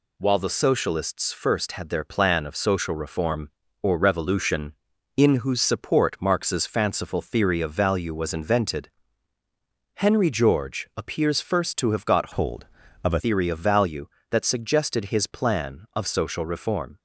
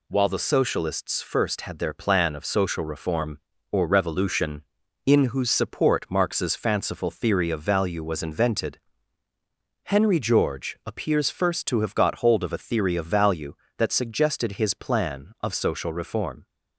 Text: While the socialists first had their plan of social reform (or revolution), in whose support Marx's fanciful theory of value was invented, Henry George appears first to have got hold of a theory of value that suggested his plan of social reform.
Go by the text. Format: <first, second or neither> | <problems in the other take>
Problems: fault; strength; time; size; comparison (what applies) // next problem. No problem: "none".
second | changes voice from "hold" to "a"; from 12.3 to 13.2 s; 0.9 s long